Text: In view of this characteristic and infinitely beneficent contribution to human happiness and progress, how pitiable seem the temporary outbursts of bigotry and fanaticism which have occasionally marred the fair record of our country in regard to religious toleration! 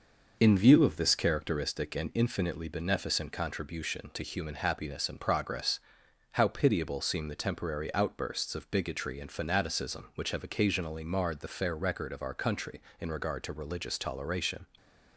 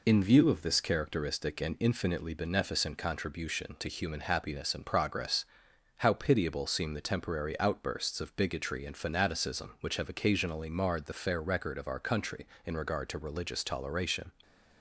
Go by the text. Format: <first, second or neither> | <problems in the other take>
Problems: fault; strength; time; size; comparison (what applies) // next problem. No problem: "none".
second | starts louder than the rest; noticeable; until 1.8 s; 5.5 dB // stays silent after the last word; slight; from 14.6 s on; 0.5 s long